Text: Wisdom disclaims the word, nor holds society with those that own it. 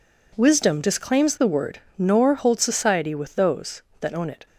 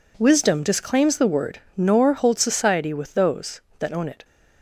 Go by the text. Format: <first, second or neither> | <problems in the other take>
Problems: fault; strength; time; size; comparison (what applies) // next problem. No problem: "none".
neither | none